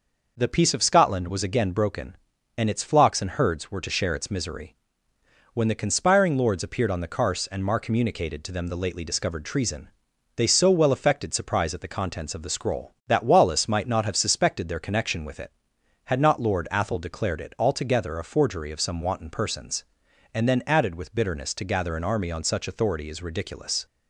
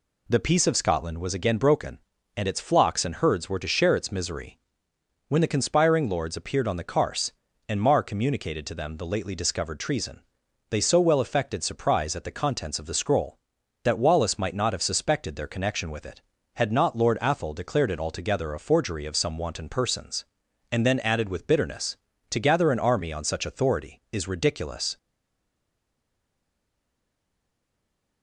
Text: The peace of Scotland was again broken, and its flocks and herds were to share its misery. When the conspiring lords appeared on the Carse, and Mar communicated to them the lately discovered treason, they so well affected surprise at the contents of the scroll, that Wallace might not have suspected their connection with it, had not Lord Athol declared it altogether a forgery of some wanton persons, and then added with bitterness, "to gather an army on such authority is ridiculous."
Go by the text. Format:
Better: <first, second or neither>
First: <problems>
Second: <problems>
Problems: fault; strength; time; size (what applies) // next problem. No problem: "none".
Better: first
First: none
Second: stays silent after the last word; strong; from 24.9 s on; 3.3 s long